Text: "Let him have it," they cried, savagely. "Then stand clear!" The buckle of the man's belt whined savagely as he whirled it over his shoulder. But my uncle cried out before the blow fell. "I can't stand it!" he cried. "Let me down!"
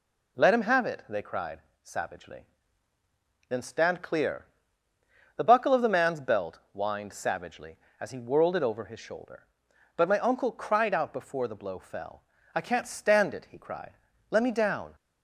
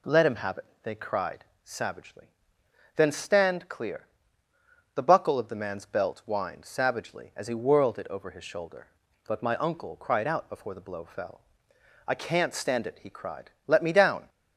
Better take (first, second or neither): neither